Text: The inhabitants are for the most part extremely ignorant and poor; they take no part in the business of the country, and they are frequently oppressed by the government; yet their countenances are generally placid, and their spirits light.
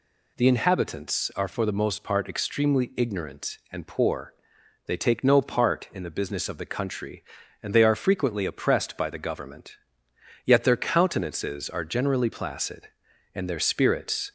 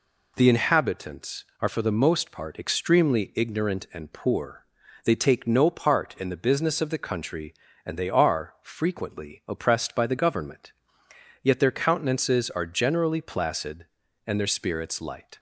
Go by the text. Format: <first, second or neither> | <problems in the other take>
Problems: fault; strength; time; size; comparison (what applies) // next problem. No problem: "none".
second | stops before "light"; at 14.2 s